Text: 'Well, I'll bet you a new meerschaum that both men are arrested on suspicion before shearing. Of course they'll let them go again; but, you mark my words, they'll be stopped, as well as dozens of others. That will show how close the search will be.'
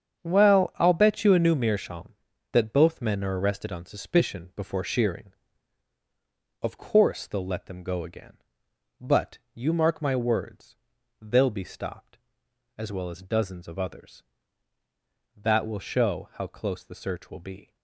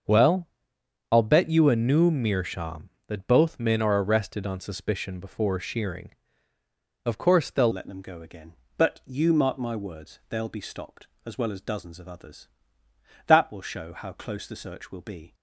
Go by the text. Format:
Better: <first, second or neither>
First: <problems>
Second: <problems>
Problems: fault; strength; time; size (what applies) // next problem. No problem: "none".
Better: first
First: starts louder than the rest; strong; until 1.2 s; 7.5 dB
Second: starts louder than the rest; until 1.7 s; 7 dB // changes voice at "let"; from 7.7 s on; 7.6 s long